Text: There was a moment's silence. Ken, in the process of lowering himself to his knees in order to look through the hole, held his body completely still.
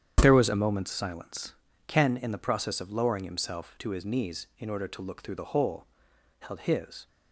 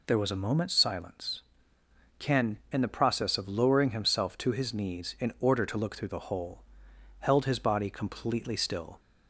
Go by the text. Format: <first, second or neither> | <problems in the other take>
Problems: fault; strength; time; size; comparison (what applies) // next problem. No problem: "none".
second | starts louder than the rest; strong; until 1.2 s; 9 dB // stops before "body completely still"; at 7.0 s